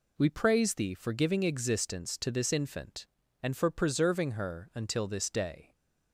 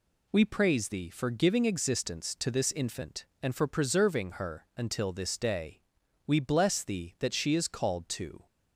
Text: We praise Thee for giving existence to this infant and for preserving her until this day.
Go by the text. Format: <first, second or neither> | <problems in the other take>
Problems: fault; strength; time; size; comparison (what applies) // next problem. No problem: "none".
first | goes on to say "We bless Thee that she is called to"; strong; from 6.2 s on; 2.2 s long